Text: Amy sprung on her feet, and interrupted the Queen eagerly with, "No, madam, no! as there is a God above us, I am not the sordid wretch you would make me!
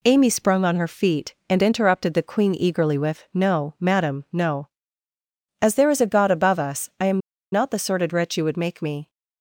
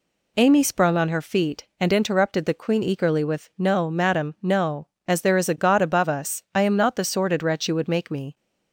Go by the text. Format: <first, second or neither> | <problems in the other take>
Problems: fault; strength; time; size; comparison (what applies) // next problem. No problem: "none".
second | pauses between "am" and "not"; slight; at 7.1 s; 0.32 s long